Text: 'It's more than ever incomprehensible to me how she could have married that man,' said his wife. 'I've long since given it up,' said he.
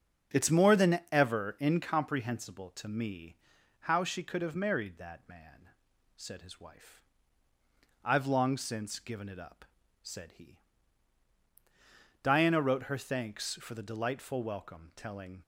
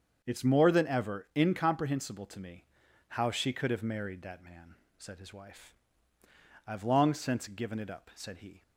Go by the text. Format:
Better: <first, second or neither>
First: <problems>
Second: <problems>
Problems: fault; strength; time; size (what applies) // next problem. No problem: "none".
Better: second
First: starts louder than the rest; strong; until 1.4 s; 7.5 dB // pauses between "me" and "how"; at 3.3 s; 0.44 s long // goes on to say "Diana wrote her thanks for the delightful welcome telling"; strong; from 12.2 s on; 3.2 s long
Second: starts louder than the rest; strong; until 1.2 s; 7 dB // pauses between "me" and "how"; noticeable; at 2.6 s; 0.46 s long